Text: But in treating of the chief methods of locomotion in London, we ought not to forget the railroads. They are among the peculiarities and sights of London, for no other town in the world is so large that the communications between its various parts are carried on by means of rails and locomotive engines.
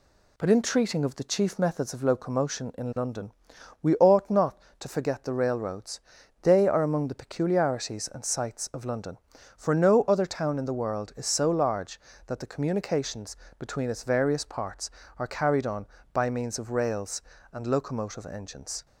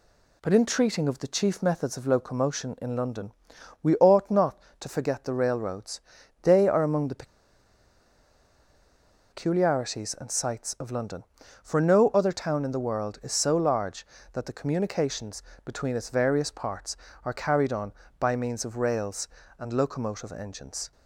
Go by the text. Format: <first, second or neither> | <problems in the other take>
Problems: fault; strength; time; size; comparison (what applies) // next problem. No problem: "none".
first | pauses between "the" and "peculiarities"; strong; at 7.2 s; 2.0 s long // pauses between "communications" and "between"; slight; at 15.4 s; 0.24 s long; slight in the first